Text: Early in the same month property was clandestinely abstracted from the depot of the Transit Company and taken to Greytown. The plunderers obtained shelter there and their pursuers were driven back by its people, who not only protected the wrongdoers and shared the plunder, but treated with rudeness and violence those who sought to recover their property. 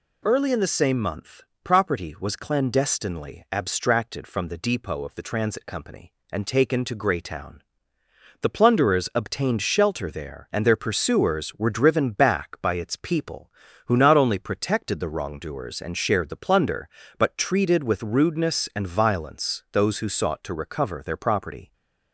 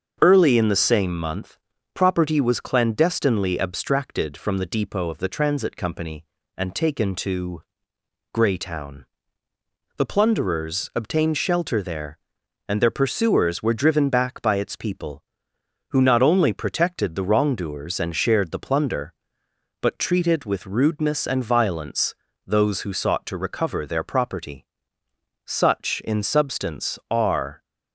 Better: first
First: pauses between "month" and "property"; slight; at 1.4 s; 0.22 s long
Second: starts louder than the rest; until 1.2 s; 6.5 dB // pauses between "month" and "property"; slight; at 1.5 s; 0.36 s long // pauses between "to" and "Greytown"; noticeable; at 7.6 s; 0.72 s long // pauses between "violence" and "those"; slight; at 22.1 s; 0.30 s long // goes on to say "Such in substance are"; strong; from 25.4 s on; 2.1 s long

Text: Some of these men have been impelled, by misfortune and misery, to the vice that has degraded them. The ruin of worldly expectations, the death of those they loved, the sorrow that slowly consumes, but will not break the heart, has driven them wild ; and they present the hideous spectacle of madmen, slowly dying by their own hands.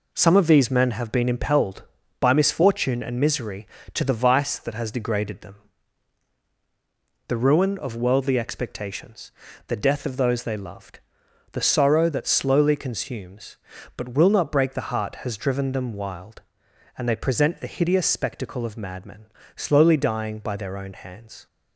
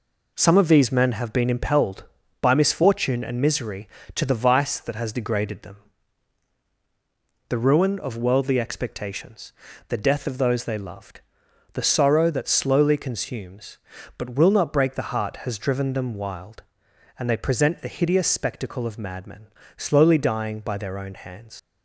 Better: first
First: none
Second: leaves "hands" unfinished; at 21.5 s; 75 ms

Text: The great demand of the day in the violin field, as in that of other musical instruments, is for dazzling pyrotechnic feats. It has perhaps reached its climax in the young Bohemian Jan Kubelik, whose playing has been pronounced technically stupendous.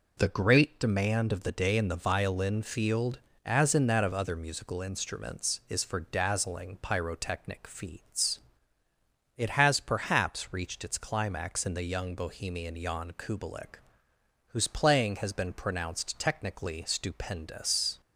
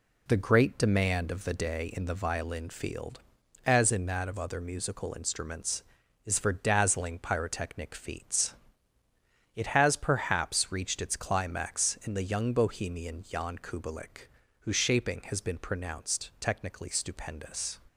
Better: first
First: none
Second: says "shaping" for "playing"; at 14.7 s

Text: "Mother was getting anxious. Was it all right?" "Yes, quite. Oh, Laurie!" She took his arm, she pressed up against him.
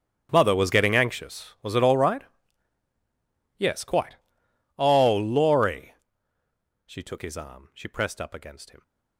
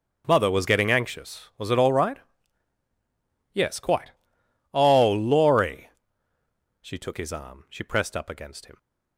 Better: second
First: gets quieter; strong; throughout; 20 dB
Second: none

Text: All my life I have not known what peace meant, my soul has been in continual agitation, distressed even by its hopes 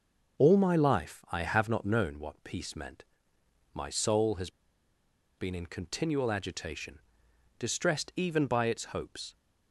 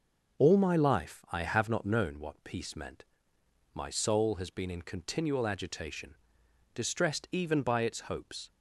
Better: second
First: pauses between "has" and "been"; noticeable; at 4.5 s; 0.87 s long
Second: none

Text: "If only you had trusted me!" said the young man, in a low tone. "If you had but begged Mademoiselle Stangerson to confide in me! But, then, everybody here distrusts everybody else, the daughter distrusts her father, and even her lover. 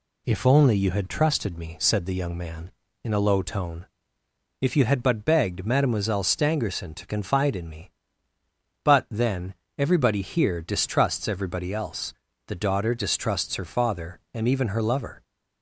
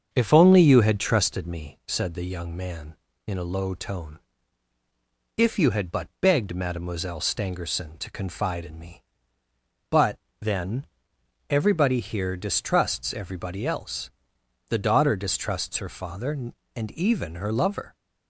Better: first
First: none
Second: starts louder than the rest; until 1.4 s; 7 dB

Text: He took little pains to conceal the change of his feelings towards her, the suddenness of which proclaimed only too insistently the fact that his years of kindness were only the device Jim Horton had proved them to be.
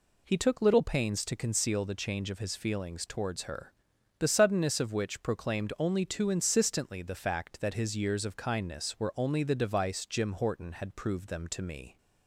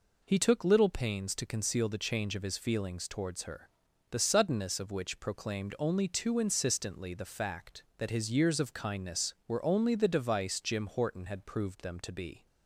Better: second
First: says "me" for "be"; at 11.6 s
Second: none

